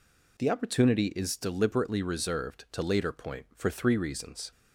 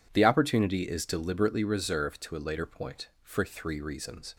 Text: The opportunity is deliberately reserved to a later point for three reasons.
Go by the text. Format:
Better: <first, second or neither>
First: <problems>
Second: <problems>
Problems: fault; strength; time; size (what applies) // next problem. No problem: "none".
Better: second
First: skips "a"; at 2.8 s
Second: none